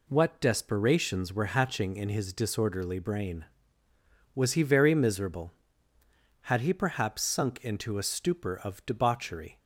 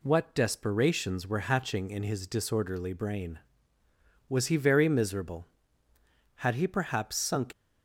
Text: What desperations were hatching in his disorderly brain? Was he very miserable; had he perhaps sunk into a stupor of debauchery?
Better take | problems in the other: first | stops before "into a stupor of debauchery"; at 7.5 s

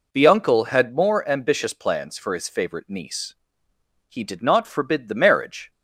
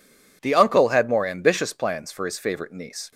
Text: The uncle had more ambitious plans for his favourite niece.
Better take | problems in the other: second | goes on to say "He did not forbid the marriage"; from 4.0 s on; 1.6 s long

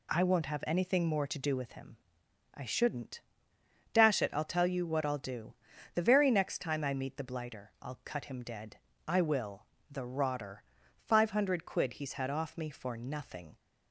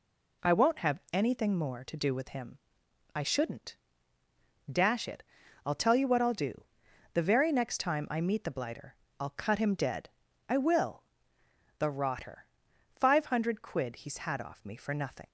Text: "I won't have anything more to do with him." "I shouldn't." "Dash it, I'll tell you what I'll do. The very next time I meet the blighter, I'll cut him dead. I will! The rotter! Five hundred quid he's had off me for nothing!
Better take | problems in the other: neither | none

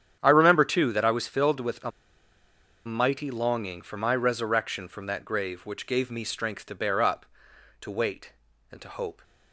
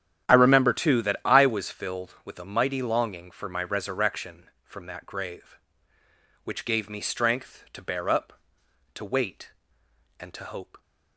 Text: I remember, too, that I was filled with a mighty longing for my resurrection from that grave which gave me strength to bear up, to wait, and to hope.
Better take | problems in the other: second | starts louder than the rest; strong; until 1.2 s; 9 dB; strong in the second // pauses between "a" and "mighty"; noticeable; at 1.9 s; 0.96 s long

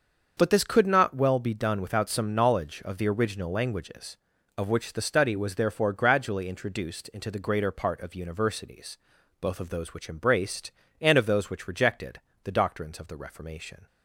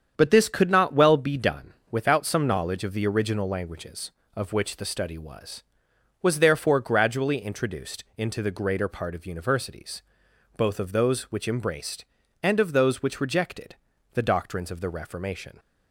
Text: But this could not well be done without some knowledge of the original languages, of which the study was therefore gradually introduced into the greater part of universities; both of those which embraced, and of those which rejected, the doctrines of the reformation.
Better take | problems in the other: first | starts louder than the rest; strong; until 1.1 s; 8 dB; also in the first // pauses between "done" and "without"; slight; at 1.7 s; 0.18 s long // says "was" twice; at 6.2 s

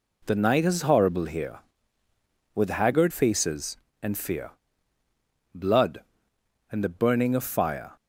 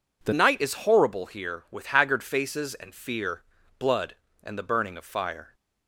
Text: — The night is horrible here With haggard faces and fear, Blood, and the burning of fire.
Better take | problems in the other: first | changes voice at "night"; from 0.3 s on; 5.2 s long

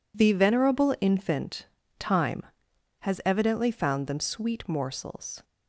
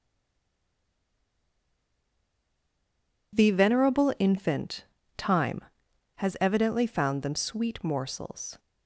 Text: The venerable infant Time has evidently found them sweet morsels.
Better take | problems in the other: first | stays silent before the first word; strong; until 3.3 s; 3.3 s long // pauses between "infant" and "Time"; slight; at 4.8 s; 0.34 s long; slight in the first

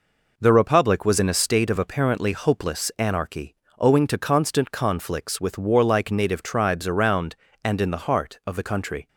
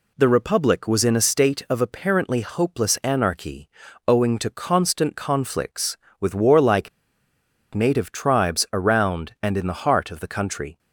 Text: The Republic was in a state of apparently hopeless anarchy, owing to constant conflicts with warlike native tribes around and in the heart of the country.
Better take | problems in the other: first | pauses between "warlike" and "native"; noticeable; at 6.8 s; 0.84 s long

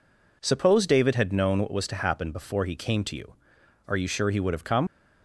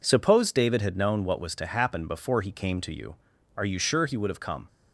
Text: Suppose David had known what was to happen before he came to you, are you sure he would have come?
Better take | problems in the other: second | leaves "come" unfinished; at 4.8 s; 100 ms

